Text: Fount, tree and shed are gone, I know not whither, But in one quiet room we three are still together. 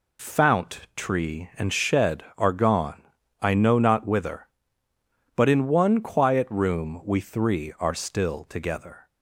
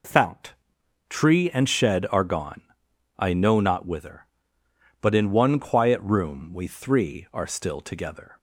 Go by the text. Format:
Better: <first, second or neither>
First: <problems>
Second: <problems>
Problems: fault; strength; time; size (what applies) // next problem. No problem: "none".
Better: neither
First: none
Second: none